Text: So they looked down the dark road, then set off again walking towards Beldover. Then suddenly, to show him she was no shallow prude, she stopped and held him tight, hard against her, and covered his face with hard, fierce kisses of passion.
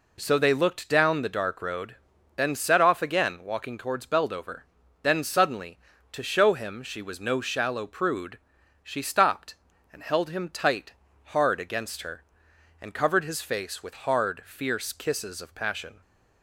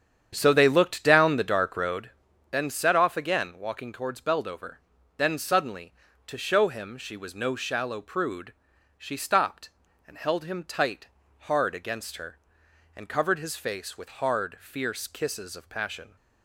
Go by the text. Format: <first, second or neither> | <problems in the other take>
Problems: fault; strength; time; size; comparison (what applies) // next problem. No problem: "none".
first | starts louder than the rest; strong; until 2.2 s; 8.5 dB